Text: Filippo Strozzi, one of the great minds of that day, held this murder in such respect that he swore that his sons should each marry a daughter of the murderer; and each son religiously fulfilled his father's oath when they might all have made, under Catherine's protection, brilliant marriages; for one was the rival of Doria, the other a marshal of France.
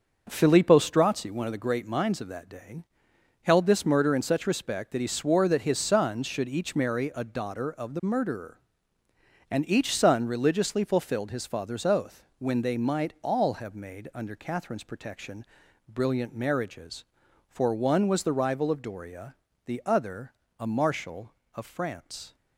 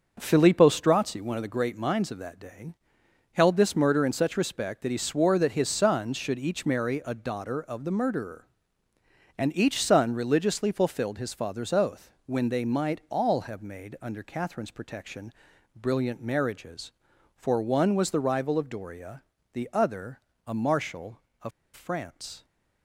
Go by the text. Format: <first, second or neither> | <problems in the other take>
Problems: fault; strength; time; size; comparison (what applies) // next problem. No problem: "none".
first | starts louder than the rest; until 1.2 s; 6.5 dB; also in the first // pauses between "oath" and "when"; slight; at 12.1 s; 0.16 s long; slight in the first // pauses between "other" and "a"; slight; at 20.1 s; 0.30 s long; slight in the first // pauses between "of" and "France"; slight; at 21.5 s; 0.24 s long